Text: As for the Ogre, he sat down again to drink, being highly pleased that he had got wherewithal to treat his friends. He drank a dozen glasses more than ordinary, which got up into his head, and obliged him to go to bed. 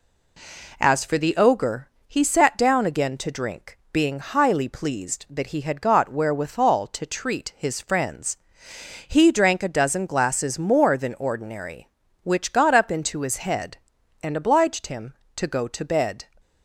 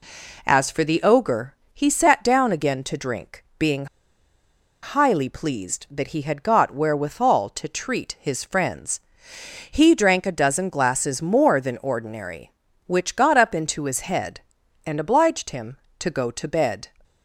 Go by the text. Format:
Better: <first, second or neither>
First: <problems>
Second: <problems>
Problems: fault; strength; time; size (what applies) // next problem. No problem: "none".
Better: first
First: none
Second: pauses between "being" and "highly"; noticeable; at 3.8 s; 0.97 s long